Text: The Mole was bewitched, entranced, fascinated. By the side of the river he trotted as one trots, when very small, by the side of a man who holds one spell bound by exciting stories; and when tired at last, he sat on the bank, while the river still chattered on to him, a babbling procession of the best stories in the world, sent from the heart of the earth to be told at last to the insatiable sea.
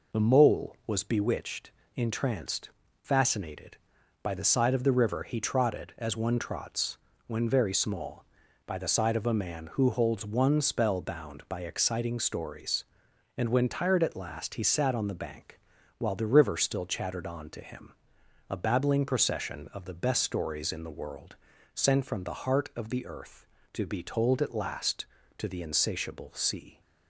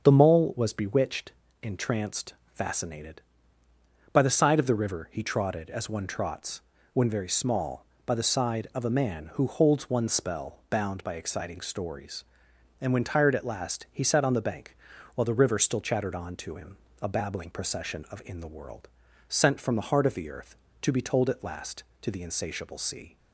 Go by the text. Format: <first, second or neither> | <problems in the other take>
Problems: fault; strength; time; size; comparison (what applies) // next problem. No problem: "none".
first | starts louder than the rest; until 1.0 s; 6.5 dB // skips "the best stories"; at 18.2 s